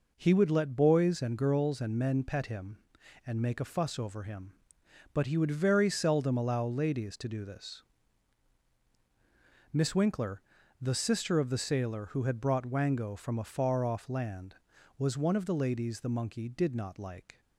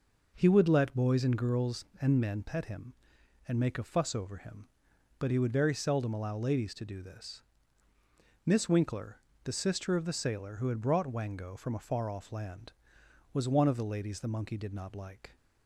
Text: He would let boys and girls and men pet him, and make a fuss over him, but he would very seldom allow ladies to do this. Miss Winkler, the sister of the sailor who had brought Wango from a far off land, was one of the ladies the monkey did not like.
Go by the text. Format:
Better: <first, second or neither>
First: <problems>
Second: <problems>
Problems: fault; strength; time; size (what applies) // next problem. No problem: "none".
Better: neither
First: none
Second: none